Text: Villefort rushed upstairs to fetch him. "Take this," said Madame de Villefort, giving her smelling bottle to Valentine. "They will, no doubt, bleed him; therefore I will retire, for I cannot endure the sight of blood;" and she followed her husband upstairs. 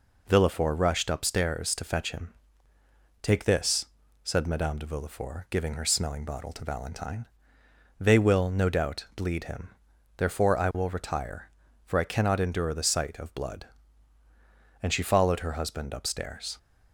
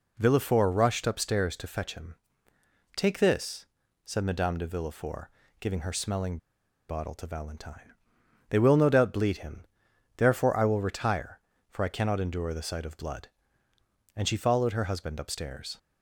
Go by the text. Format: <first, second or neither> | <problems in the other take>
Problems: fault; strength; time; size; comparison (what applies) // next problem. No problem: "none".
first | pauses between "smelling" and "bottle"; noticeable; at 6.3 s; 0.52 s long